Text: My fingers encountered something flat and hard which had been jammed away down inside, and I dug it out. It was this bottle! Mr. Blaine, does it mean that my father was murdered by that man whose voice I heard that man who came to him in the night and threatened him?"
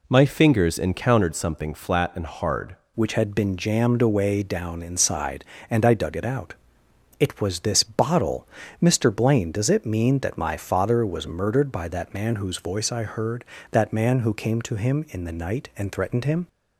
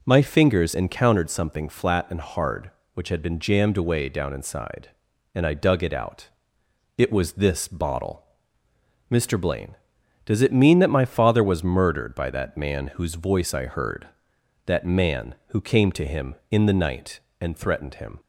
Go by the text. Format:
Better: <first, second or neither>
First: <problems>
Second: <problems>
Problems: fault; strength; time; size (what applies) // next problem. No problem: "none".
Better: second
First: changes voice at "which"; from 2.9 s on; 13.5 s long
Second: none